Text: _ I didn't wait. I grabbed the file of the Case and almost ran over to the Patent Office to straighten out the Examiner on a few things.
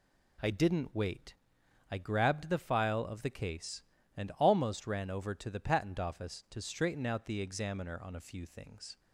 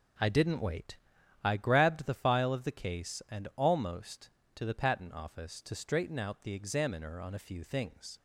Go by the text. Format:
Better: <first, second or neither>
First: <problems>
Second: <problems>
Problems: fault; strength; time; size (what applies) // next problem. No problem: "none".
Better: first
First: none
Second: skips "ran over"; at 4.4 s